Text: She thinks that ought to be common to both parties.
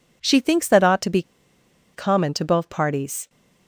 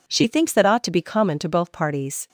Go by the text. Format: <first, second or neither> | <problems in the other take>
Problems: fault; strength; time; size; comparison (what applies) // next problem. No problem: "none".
second | pauses between "be" and "common"; noticeable; at 1.2 s; 0.72 s long